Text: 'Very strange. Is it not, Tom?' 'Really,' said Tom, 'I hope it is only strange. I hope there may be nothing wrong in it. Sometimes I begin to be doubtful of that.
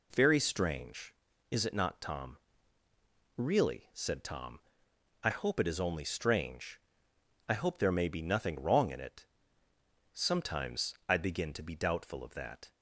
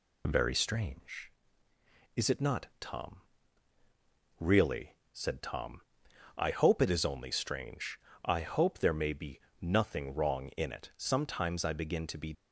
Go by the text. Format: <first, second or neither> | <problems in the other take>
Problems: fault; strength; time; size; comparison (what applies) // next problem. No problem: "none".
first | pauses between "be" and "nothing"; slight; at 9.3 s; 0.22 s long // stops before "doubtful of that"; at 12.3 s